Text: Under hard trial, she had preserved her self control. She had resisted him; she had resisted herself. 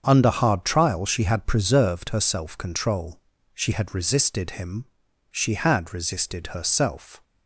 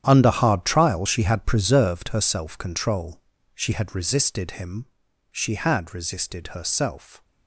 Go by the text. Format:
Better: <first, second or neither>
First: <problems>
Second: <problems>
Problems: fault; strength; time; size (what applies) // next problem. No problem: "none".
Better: first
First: starts louder than the rest; until 1.0 s; 7 dB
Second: gets quieter; strong; throughout; 13.5 dB // starts louder than the rest; strong; until 1.0 s; 10 dB